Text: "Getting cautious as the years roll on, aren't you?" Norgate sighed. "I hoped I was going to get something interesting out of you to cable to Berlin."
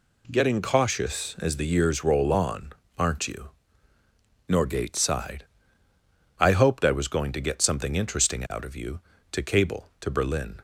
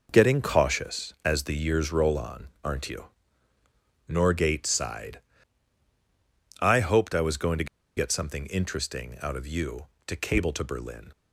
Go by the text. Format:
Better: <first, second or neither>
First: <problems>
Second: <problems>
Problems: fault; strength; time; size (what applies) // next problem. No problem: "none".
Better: first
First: none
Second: pauses between "to" and "get"; slight; at 7.6 s; 0.31 s long